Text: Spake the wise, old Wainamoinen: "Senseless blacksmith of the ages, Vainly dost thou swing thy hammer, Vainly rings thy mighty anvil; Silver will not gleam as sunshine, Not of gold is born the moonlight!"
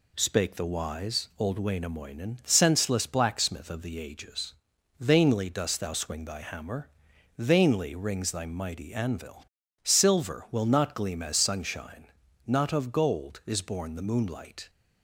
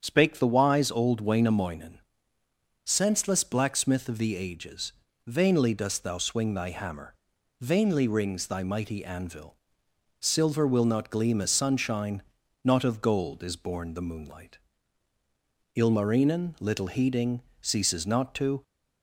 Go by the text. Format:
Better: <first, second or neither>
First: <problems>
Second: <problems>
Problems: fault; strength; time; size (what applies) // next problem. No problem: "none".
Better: first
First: none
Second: starts louder than the rest; strong; until 1.0 s; 8 dB // goes on to say "Ilmarinen little heeding Ceases not to"; strong; from 15.7 s on; 2.8 s long